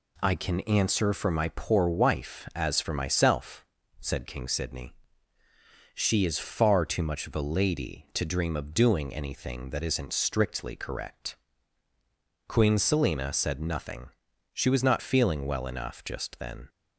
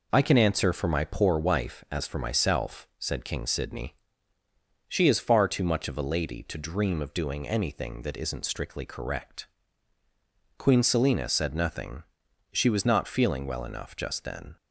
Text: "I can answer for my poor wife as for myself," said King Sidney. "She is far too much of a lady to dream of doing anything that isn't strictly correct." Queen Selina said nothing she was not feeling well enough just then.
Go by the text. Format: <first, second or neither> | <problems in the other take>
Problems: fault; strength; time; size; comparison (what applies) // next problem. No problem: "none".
neither | pauses between "nothing" and "she"; the same in both